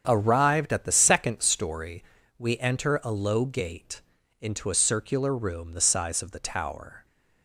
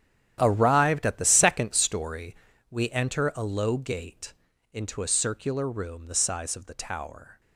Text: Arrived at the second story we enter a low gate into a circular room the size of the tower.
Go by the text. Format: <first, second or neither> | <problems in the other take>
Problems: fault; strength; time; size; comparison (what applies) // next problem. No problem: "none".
first | gets quieter; strong; throughout; 14.5 dB // starts louder than the rest; strong; until 1.4 s; 10.5 dB; strong in the first // pauses between "story" and "we"; slight; at 2.3 s; 0.34 s long; slight in the first // pauses between "gate" and "into"; at 4.3 s; 0.38 s long; also in the first